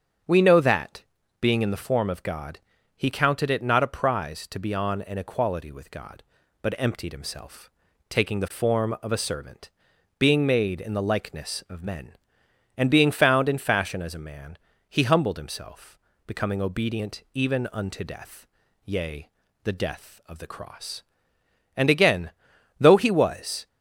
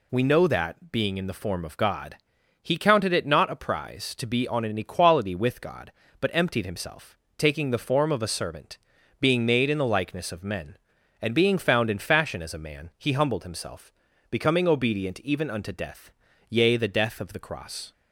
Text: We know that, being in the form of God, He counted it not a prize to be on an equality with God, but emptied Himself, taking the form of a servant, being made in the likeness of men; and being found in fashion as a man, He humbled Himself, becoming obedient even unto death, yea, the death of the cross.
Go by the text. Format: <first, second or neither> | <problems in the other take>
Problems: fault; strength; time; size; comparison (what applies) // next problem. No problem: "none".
second | starts louder than the rest; strong; until 1.6 s; 7 dB // goes on to say "And again though He was"; strong; from 21.7 s on; 1.9 s long